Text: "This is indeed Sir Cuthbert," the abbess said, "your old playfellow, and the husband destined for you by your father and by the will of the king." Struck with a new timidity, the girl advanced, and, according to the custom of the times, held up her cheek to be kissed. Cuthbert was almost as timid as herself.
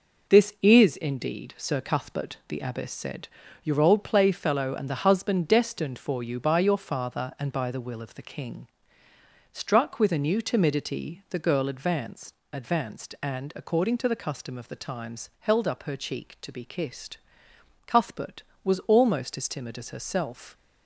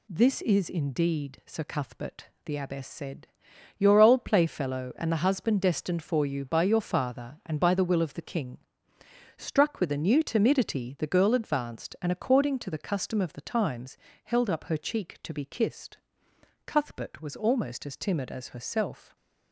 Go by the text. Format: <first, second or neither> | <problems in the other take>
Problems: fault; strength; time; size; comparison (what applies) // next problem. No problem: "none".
second | says "advanced" twice; at 12.5 s